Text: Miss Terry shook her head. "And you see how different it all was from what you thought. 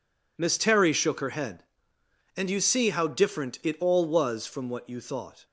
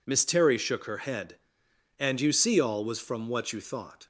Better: first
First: none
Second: skips "how different it"; at 2.5 s

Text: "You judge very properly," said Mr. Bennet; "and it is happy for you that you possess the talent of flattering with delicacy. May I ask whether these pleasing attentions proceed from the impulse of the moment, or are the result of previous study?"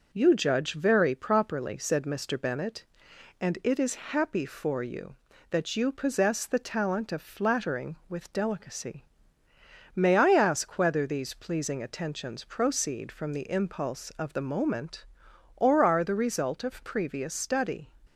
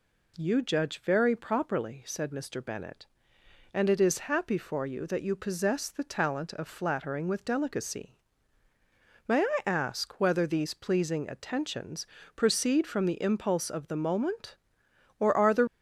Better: first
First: none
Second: pauses between "attentions" and "proceed"; slight; at 12.0 s; 0.30 s long // stops before "result of previous study"; at 15.6 s

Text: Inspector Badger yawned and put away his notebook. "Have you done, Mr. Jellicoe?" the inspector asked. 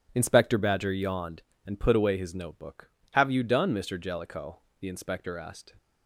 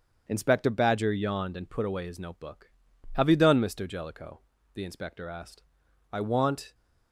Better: first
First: starts louder than the rest; strong; until 1.1 s; 7.5 dB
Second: starts louder than the rest; strong; until 1.2 s; 7.5 dB // goes on to say "I want"; noticeable; from 6.1 s on; 0.62 s long

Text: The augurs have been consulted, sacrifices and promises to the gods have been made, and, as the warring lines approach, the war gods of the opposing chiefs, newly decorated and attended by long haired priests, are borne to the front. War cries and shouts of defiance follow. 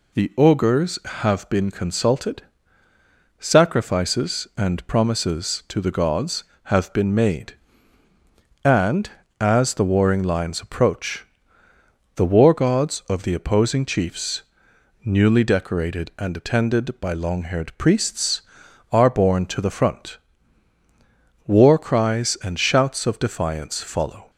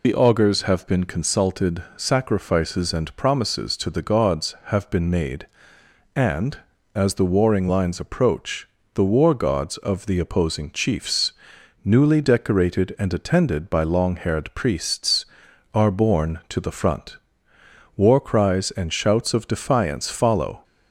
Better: first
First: none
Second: loses the start of "The"; at 0.0 s; 50 ms

